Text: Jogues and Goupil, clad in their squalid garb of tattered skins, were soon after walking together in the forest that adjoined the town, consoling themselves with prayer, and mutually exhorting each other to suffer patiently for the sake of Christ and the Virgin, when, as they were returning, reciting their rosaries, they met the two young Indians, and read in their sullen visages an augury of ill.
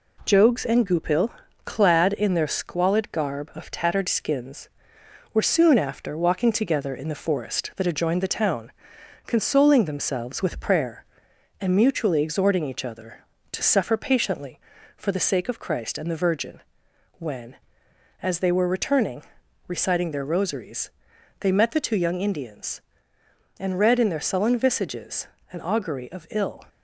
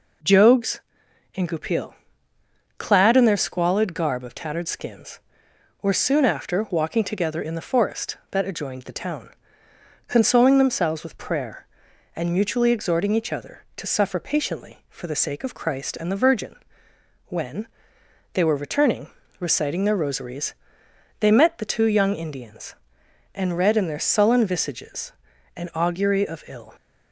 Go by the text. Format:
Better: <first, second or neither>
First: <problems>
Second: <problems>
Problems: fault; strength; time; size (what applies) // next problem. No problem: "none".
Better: first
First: pauses between "visages" and "an"; slight; at 25.2 s; 0.24 s long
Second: skips "as"; at 18.0 s // pauses between "visages" and "an"; at 25.1 s; 0.44 s long